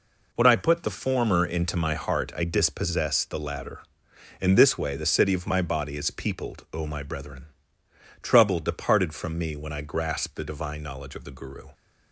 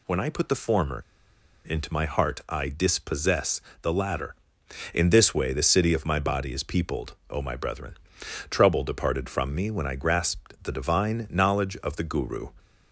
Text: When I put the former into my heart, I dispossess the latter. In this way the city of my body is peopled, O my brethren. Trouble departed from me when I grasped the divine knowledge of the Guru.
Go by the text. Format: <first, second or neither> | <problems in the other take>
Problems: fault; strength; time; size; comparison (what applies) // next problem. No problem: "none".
first | pauses between "former" and "into"; noticeable; at 1.0 s; 0.65 s long // pauses between "dispossess" and "the"; slight; at 3.6 s; 0.22 s long